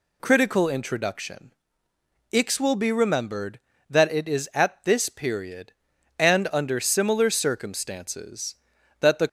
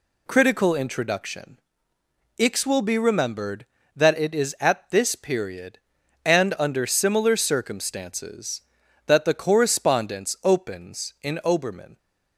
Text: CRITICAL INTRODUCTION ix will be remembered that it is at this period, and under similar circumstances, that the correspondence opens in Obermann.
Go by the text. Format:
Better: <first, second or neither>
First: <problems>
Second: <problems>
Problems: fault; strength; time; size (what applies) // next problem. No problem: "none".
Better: second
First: pauses between "INTRODUCTION" and "ix"; noticeable; at 1.5 s; 0.80 s long // stops before "correspondence opens in Obermann"; at 9.2 s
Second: pauses between "INTRODUCTION" and "ix"; noticeable; at 1.5 s; 0.80 s long